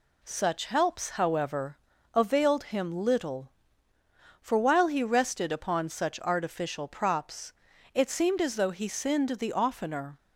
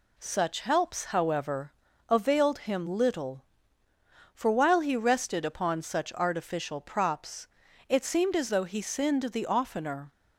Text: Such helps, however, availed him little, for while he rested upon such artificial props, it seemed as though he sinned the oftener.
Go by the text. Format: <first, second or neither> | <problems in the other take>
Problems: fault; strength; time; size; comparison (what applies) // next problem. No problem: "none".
neither | none